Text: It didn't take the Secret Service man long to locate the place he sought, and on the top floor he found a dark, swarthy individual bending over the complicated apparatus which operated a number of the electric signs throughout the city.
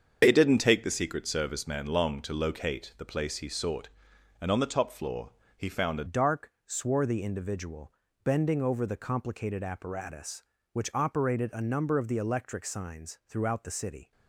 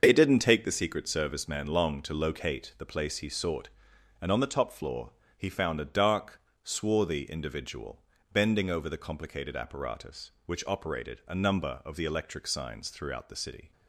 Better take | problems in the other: second | starts louder than the rest; until 1.2 s; 7 dB; also in the second // pauses between "floor" and "he"; slight; at 5.3 s; 0.26 s long; slight in the second // changes voice at "dark"; from 6.0 s on; 8.1 s long // pauses between "individual" and "bending"; slight; at 7.9 s; 0.32 s long; slight in the second

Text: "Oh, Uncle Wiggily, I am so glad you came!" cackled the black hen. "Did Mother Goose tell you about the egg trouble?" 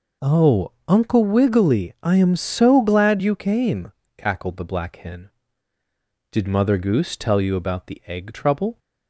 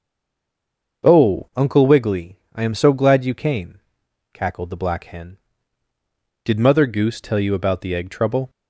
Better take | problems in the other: first | stays silent before the first word; until 1.0 s; 1.0 s long // starts louder than the rest; noticeable; until 2.1 s; 6 dB

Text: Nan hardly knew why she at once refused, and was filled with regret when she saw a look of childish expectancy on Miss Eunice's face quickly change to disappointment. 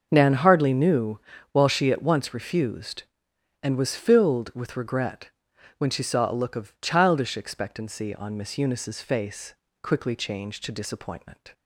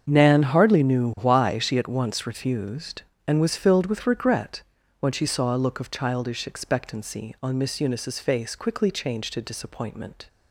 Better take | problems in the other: second | starts louder than the rest; until 1.1 s; 6 dB; strong in the second // says "while" for "why"; at 1.5 s // pauses between "regret" and "when"; noticeable; at 5.2 s; 0.48 s long; also in the second // pauses between "face" and "quickly"; slight; at 9.5 s; 0.28 s long

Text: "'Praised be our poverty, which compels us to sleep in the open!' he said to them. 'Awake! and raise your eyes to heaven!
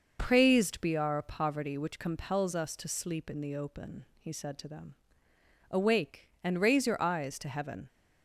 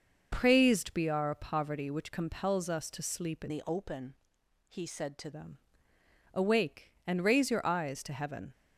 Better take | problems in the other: first | changes voice from "the" to "to"; from 3.4 to 5.3 s; 1.9 s long

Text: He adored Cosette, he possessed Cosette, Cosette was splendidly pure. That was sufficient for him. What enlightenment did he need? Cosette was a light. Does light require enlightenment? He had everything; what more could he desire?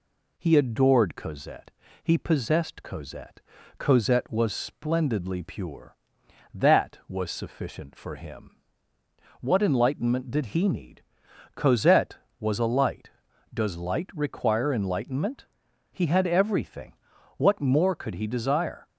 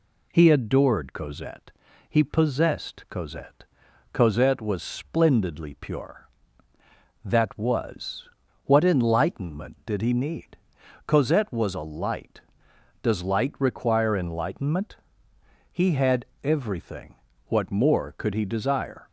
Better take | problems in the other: first | skips "sufficient for him"; at 8.4 s // pauses between "had" and "everything"; slight; at 16.2 s; 0.18 s long

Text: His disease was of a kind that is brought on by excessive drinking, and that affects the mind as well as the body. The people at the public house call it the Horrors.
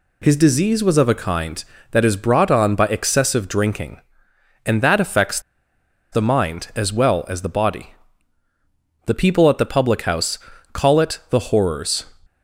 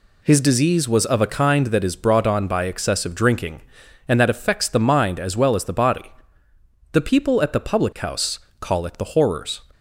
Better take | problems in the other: second | pauses between "affects" and "the"; noticeable; at 5.4 s; 0.71 s long // pauses between "house" and "call"; at 10.3 s; 0.38 s long; slight in the second

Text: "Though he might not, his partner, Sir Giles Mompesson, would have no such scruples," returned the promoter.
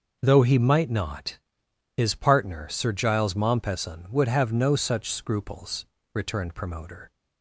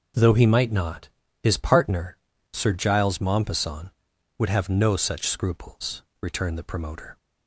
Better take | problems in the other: second | skips "the"; at 6.5 s

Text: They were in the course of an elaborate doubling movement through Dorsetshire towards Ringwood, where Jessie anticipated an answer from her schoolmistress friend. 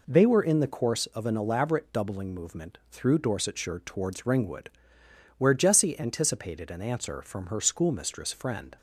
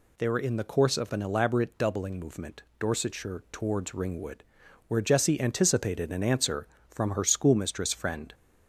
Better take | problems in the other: first | skips "through"; at 2.7 s

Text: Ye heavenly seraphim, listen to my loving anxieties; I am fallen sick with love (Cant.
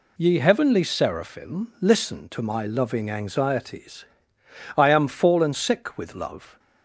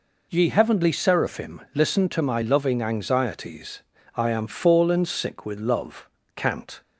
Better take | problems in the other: second | stops before "Cant"; at 6.5 s

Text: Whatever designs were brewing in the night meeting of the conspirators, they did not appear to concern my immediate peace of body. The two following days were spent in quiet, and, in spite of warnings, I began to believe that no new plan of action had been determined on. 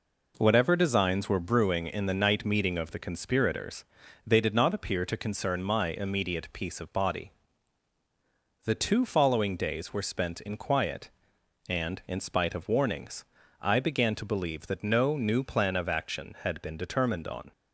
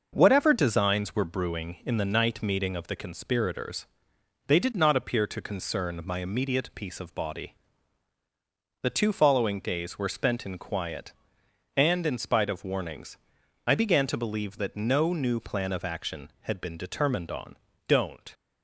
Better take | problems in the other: first | goes on to say "Don't"; slight; from 17.8 s on; 0.46 s long

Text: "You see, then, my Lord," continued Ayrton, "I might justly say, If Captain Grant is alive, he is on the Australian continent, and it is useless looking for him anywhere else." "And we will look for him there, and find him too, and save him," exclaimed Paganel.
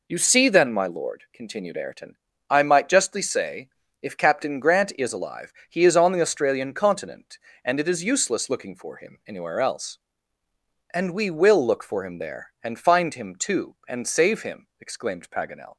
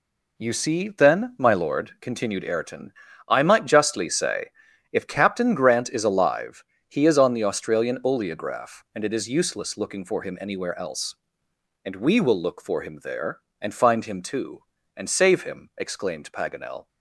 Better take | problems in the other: first | says "oleograph" for "continent"; at 8.0 s

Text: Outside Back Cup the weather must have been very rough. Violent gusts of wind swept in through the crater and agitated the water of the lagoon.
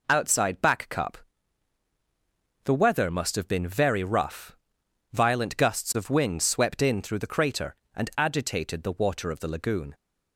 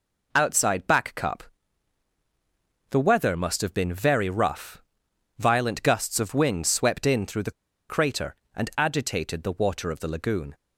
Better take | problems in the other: first | pauses between "Cup" and "the"; strong; at 1.4 s; 1.4 s long; strong in the first // pauses between "the" and "crater"; at 7.5 s; 0.38 s long

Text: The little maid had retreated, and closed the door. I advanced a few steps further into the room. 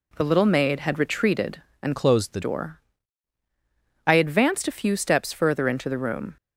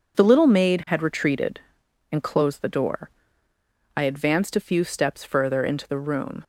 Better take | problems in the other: second | changes voice from "closed" to "the"; from 1.9 to 2.4 s; 0.5 s long

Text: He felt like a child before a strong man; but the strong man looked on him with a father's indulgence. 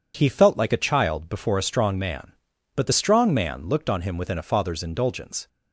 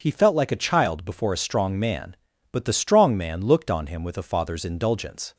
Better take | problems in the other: second | says "within" for "with"; at 4.1 s

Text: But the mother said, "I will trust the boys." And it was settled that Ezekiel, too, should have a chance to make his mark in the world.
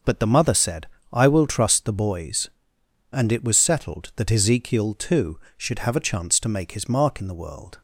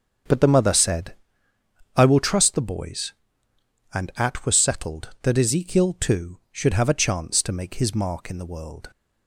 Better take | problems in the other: first | starts louder than the rest; until 2.0 s; 7 dB; noticeable in the first // says "at" for "it"; at 4.1 s

